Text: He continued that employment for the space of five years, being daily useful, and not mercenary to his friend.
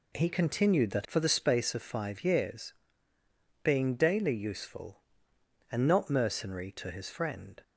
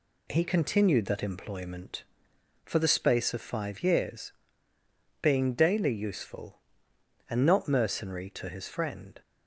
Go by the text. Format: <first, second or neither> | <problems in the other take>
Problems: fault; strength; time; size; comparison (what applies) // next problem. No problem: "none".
second | skips "employment"; at 1.0 s